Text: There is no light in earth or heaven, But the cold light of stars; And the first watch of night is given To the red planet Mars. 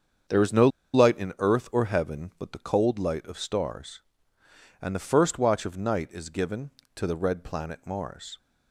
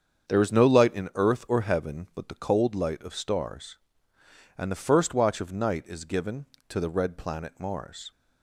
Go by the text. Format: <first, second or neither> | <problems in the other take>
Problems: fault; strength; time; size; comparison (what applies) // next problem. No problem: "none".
second | starts louder than the rest; strong; until 1.6 s; 7.5 dB; strong in the second // pauses between "no" and "light"; slight; at 0.6 s; 0.25 s long